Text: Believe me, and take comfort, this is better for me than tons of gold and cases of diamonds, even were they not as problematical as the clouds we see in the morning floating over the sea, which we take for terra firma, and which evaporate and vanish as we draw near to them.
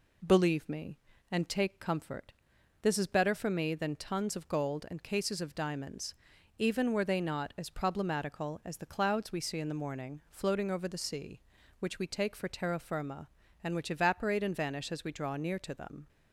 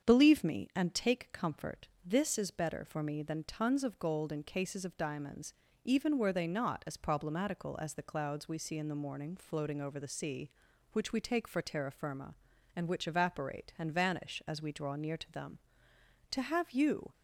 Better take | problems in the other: first | starts louder than the rest; strong; until 1.1 s; 7.5 dB // goes on to say "To have you"; noticeable; from 16.3 s on; 0.82 s long

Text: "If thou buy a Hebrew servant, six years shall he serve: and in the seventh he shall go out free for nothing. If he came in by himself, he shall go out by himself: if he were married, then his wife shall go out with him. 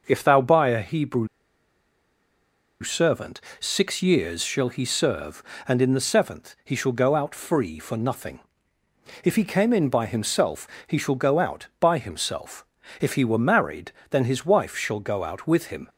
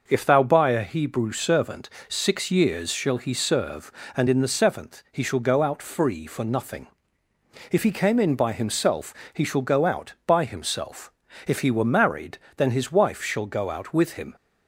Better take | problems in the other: second | pauses between "Hebrew" and "servant"; strong; at 1.2 s; 1.5 s long

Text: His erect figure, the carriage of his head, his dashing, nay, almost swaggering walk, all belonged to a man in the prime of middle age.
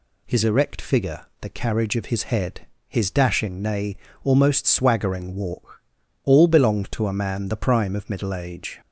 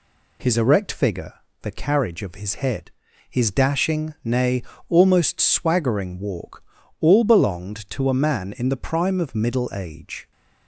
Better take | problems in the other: second | skips "in"; at 7.4 s

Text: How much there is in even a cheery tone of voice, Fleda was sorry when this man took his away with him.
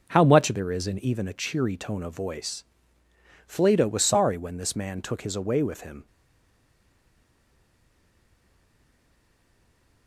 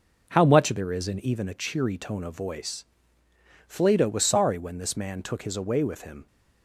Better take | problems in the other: second | stays silent after the last word; strong; from 6.0 s on; 4.0 s long

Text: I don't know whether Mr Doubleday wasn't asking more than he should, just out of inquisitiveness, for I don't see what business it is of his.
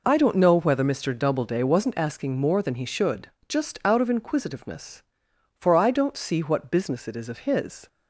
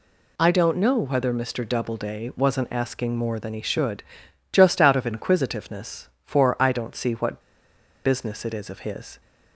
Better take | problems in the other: first | pauses between "what" and "business"; noticeable; at 7.3 s; 0.65 s long

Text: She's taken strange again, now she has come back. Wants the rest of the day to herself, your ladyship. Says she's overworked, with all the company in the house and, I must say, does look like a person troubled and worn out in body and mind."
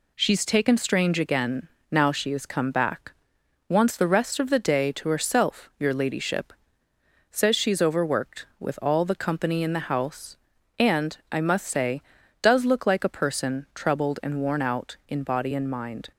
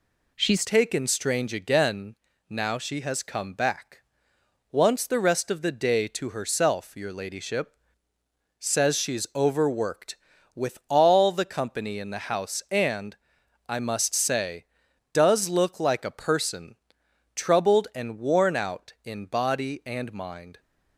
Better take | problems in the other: first | changes voice at "taken"; from 0.6 s on; 19.9 s long // pauses between "person" and "troubled"; noticeable; at 16.7 s; 0.58 s long

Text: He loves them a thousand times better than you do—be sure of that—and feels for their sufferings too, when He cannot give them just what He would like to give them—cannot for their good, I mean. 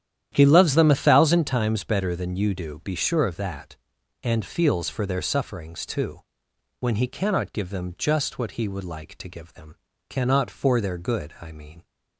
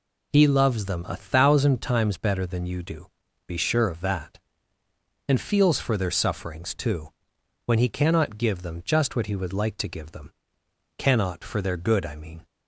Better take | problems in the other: second | starts louder than the rest; strong; until 1.5 s; 10.5 dB

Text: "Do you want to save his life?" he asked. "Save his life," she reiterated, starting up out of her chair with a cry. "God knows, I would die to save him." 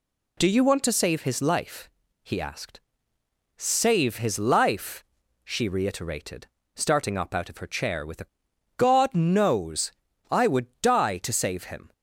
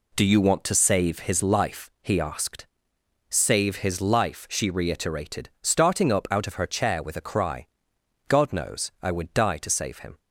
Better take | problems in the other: second | skips "cry"; at 8.5 s // pauses between "would" and "die"; slight; at 10.6 s; 0.16 s long

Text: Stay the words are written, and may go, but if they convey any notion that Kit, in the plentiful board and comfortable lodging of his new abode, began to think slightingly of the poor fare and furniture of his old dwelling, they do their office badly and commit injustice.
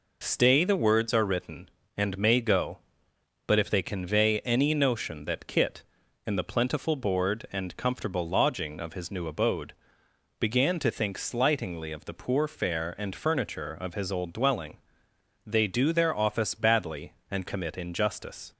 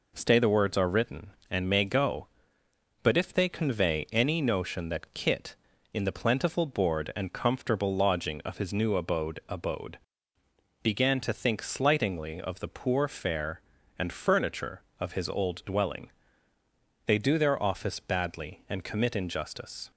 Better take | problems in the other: first | says "abode" twice; at 9.4 s

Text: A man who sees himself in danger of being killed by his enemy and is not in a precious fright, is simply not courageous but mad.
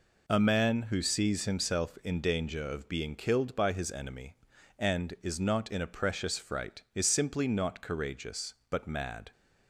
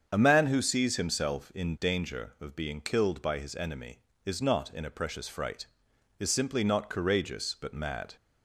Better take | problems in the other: first | starts louder than the rest; strong; until 1.1 s; 7 dB // skips "and"; at 4.1 s

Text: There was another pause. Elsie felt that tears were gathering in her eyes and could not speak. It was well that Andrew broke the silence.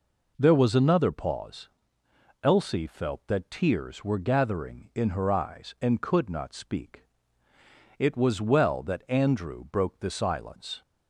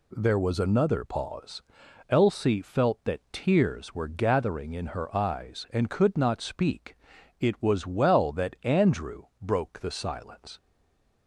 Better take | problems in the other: first | pauses between "Andrew" and "broke"; slight; at 9.2 s; 0.16 s long // stays silent after the last word; slight; from 10.5 s on; 0.7 s long

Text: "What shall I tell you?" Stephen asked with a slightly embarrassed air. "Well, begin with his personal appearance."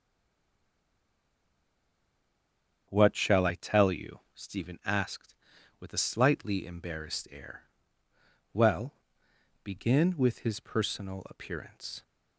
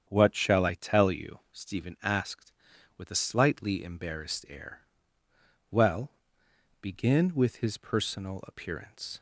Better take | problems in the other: second | stays silent before the first word; strong; until 2.8 s; 2.8 s long // starts louder than the rest; strong; until 3.9 s; 8 dB; strong in the second

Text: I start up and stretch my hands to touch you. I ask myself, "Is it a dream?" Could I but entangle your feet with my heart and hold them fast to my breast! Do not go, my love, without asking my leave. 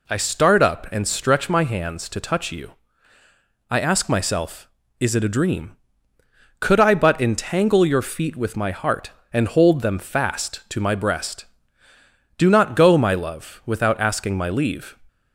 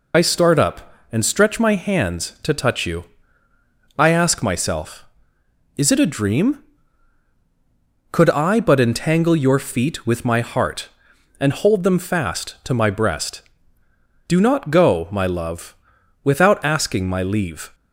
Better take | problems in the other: first | loses the start of "I"; at 0.1 s; 70 ms

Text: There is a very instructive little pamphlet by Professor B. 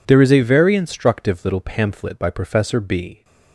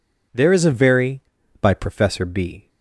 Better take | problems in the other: first | skips "instructive little pamphlet"; at 1.4 s

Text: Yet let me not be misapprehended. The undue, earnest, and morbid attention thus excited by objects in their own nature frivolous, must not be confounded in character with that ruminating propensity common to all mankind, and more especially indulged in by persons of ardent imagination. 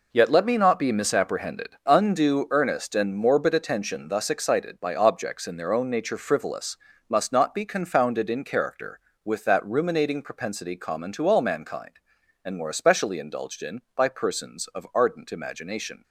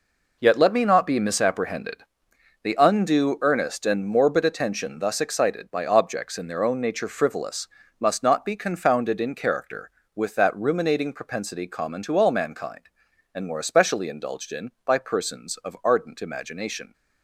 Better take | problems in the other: second | skips "The"; at 1.8 s

